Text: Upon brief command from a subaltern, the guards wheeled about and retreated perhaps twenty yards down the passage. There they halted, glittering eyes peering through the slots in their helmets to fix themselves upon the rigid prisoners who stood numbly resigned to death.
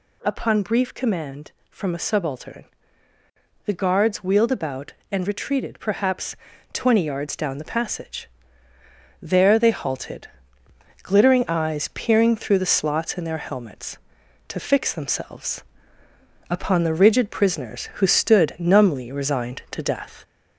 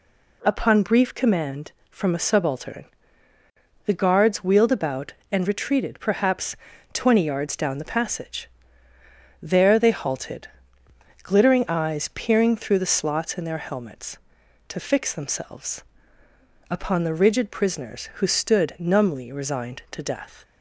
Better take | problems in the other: second | gets louder; slight; throughout; 3 dB // pauses between "perhaps" and "twenty"; at 6.3 s; 0.38 s long; also in the second // pauses between "themselves" and "upon"; noticeable; at 15.6 s; 0.88 s long; noticeable in the second

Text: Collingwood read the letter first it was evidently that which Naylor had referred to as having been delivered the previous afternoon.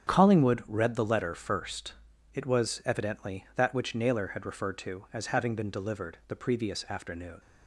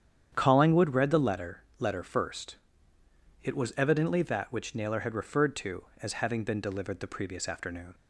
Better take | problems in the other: first | starts louder than the rest; strong; until 1.3 s; 9 dB; strong in the first // says "letter" twice; at 1.7 s // pauses between "first" and "it"; noticeable; at 2.5 s; 0.86 s long; also in the first

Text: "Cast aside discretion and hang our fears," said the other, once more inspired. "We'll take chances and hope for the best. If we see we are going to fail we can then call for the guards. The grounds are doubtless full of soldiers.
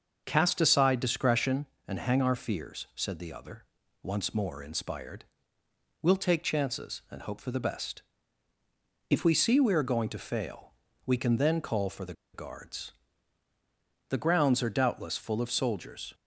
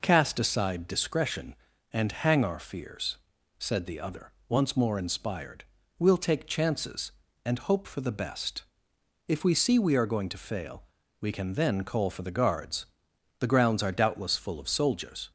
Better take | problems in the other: second | starts louder than the rest; until 1.2 s; 6.5 dB // pauses between "fail" and "we"; slight; at 10.6 s; 0.34 s long; slight in the second // pauses between "the" and "guards"; slight; at 12.1 s; 0.19 s long

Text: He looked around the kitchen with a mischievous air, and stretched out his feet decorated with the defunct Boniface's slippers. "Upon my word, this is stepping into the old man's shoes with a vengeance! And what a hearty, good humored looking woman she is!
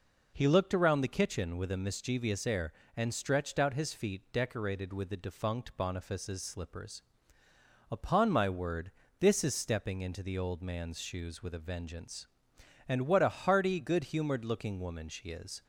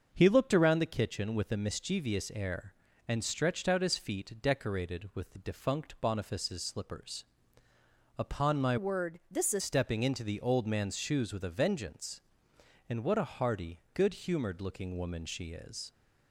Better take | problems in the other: first | starts louder than the rest; until 1.1 s; 6.5 dB // changes voice from "word" to "is"; from 8.7 to 9.6 s; 0.9 s long

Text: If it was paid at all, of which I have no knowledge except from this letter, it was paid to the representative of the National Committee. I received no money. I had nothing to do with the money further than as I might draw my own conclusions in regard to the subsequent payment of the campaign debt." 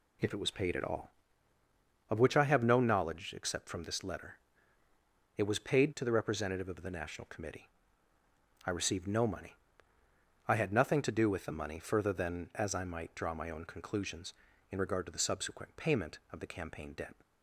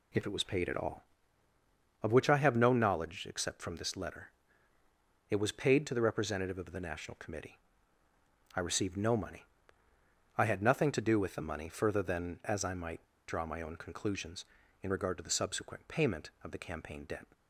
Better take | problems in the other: first | pauses between "might" and "draw"; slight; at 13.0 s; 0.21 s long

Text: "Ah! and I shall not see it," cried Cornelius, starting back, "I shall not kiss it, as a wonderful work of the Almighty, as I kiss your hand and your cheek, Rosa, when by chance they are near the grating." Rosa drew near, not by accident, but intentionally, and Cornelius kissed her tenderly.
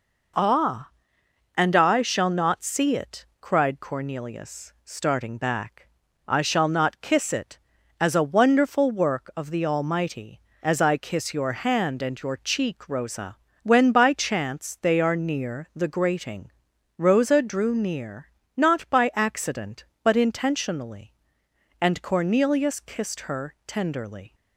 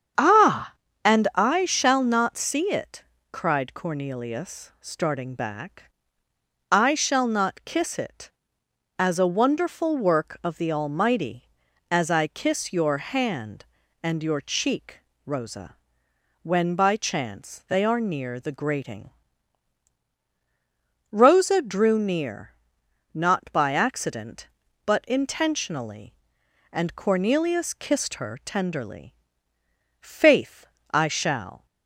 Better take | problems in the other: first | starts louder than the rest; strong; until 1.5 s; 8 dB // goes on to say "Faith I shall"; from 30.0 s on; 1.6 s long

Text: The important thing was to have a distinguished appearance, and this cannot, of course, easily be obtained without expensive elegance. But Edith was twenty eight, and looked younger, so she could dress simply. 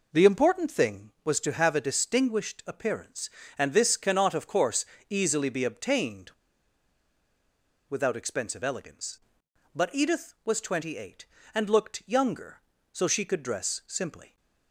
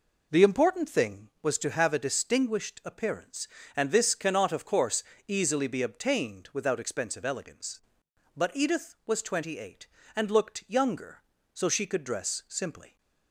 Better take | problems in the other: second | pauses between "obtained" and "without"; strong; at 6.3 s; 1.5 s long

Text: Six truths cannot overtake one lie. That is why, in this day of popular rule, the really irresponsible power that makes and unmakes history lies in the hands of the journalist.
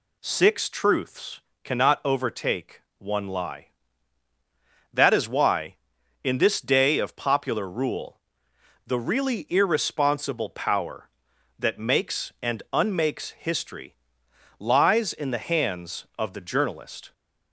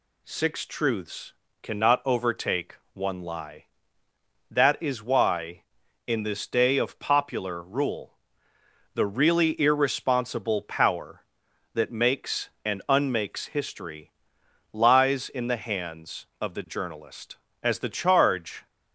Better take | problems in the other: first | pauses between "truths" and "cannot"; slight; at 1.3 s; 0.28 s long; slight in the first // pauses between "overtake" and "one"; slight; at 2.7 s; 0.18 s long; slight in the first // pauses between "history" and "lies"; noticeable; at 14.1 s; 0.60 s long; noticeable in the first // goes on to say "As the charge"; noticeable; from 17.6 s on; 1.0 s long

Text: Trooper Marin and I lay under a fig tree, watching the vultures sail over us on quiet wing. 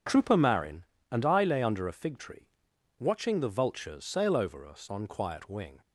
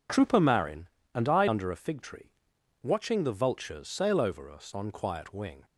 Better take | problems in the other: first | skips "lay"; at 1.4 s

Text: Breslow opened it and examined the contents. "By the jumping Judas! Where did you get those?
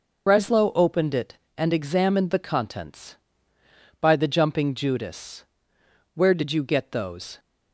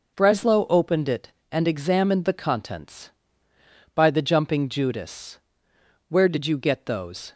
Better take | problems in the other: second | loses the start of "Breslow"; at 0.2 s; 55 ms

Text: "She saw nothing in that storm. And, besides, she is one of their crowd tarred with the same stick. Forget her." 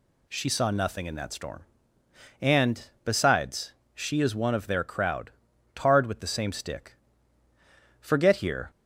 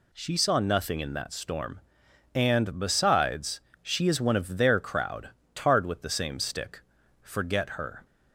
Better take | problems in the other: second | pauses between "crowd" and "tarred"; at 5.3 s; 0.44 s long; slight in the second // says "here" for "her"; at 8.3 s

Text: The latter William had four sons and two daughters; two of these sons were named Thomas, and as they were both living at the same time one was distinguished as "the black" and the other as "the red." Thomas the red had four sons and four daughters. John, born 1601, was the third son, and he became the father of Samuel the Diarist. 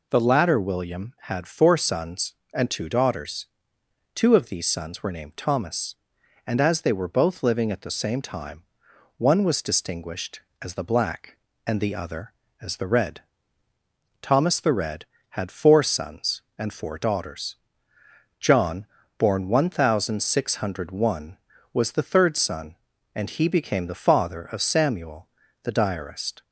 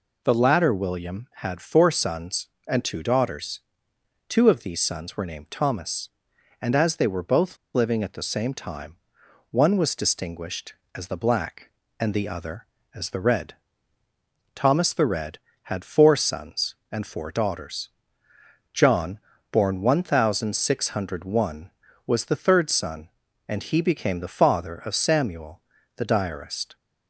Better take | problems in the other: first | pauses between "both" and "living"; slight; at 7.5 s; 0.17 s long // pauses between "time" and "one"; noticeable; at 8.9 s; 0.52 s long; noticeable in the first // pauses between "Samuel" and "the"; slight; at 25.6 s; 0.32 s long; slight in the first

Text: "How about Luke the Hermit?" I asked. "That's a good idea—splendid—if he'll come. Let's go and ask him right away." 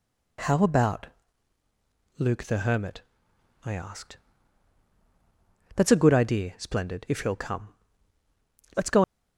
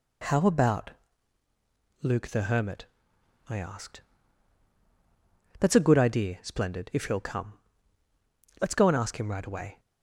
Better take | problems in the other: second | pauses between "about" and "Luke"; at 1.0 s; 1.0 s long; also in the second // stops before "and ask him right away"; at 9.0 s

